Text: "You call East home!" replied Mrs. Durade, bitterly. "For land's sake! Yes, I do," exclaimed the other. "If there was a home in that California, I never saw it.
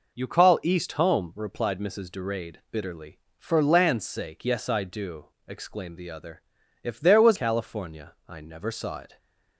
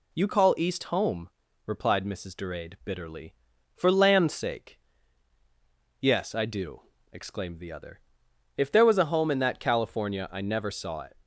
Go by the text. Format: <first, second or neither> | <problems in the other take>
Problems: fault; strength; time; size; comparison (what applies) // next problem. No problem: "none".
second | skips "a home in that"; at 7.3 s